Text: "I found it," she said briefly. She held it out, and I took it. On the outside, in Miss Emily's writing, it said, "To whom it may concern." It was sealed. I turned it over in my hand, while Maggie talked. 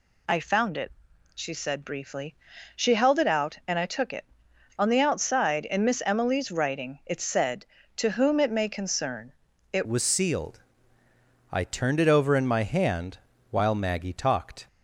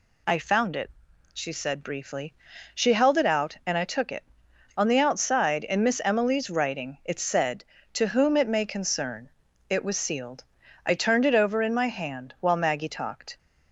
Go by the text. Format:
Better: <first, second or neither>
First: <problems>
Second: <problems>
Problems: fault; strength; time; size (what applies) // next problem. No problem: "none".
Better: second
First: changes voice at "was"; from 9.8 s on; 4.8 s long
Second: none